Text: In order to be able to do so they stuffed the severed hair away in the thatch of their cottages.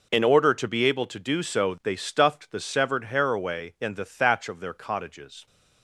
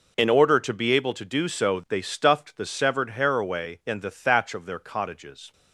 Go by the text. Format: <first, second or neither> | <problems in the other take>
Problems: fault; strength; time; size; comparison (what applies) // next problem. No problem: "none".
neither | none